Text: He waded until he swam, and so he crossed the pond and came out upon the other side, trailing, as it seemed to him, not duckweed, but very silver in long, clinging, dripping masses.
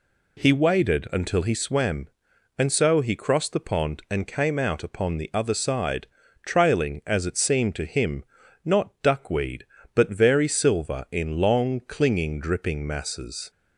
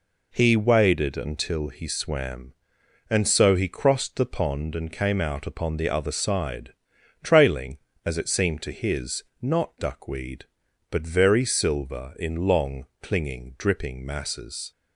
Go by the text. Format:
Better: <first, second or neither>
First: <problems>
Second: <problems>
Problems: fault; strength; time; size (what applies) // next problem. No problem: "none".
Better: first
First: none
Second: says "his" for "him"; at 8.7 s